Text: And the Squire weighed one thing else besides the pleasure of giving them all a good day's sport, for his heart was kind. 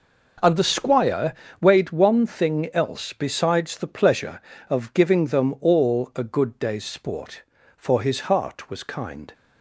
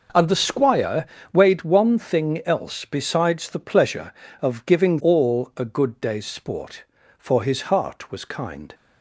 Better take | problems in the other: first | pauses between "Squire" and "weighed"; slight; at 1.0 s; 0.26 s long; slight in the first // skips "them"; at 4.9 s

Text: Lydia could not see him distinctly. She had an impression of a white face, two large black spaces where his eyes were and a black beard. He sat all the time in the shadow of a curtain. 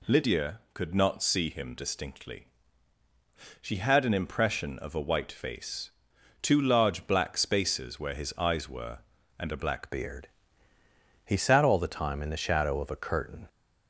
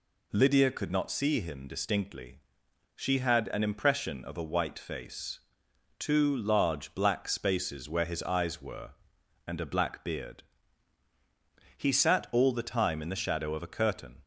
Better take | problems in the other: second | changes voice at "beard"; from 9.8 s on; 3.6 s long

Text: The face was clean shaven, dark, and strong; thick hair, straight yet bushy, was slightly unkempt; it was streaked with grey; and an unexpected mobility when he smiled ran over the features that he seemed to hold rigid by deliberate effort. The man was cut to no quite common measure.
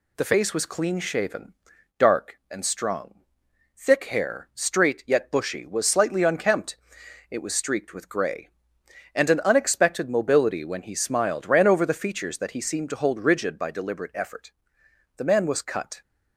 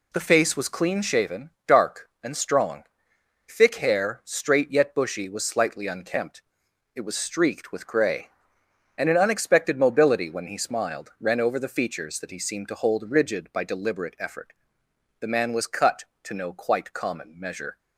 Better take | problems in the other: second | stops before "to no quite common measure"; at 16.0 s

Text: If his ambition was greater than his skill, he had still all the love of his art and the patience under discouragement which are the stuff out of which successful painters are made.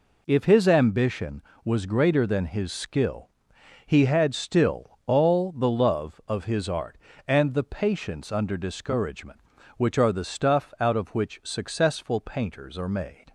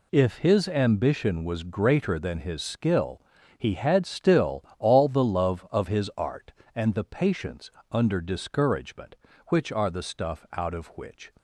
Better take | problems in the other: first | pauses between "still" and "all"; slight; at 4.6 s; 0.16 s long // pauses between "patience" and "under"; slight; at 7.6 s; 0.22 s long // stops before "successful painters are made"; at 11.3 s

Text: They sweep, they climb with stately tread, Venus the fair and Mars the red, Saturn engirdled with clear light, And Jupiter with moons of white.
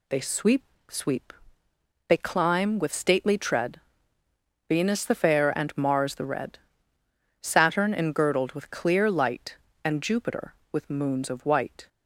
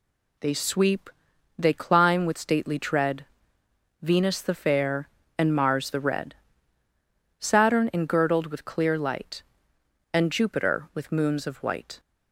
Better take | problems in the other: second | says "sweep" twice; at 0.8 s

